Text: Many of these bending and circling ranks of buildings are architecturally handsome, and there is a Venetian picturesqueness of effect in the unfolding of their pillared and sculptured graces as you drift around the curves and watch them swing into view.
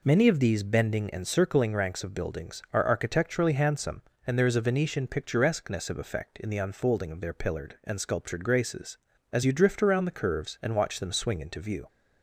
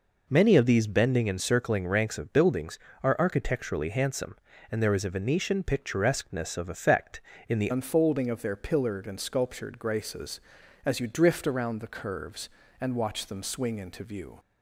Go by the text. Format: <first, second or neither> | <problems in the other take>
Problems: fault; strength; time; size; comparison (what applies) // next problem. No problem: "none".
first | changes voice at "unfolding"; from 7.7 s on; 6.6 s long